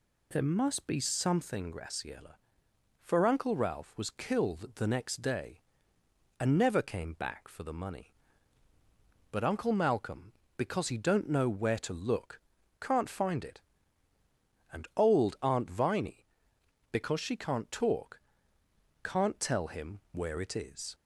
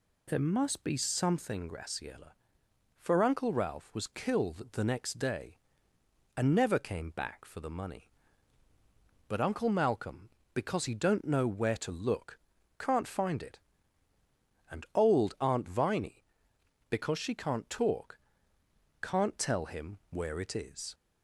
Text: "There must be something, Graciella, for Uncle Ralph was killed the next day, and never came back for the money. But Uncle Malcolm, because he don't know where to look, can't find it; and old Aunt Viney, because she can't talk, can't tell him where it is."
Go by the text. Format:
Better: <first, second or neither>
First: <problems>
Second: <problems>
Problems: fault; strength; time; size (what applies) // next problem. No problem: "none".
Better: neither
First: none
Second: none